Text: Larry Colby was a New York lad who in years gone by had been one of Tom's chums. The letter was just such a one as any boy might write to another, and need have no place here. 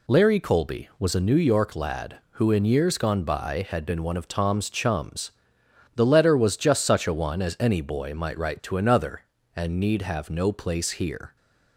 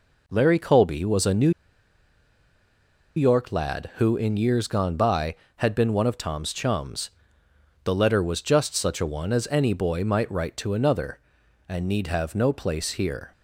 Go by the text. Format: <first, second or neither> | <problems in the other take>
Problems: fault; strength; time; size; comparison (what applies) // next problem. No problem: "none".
first | pauses between "New" and "York"; strong; at 1.5 s; 1.6 s long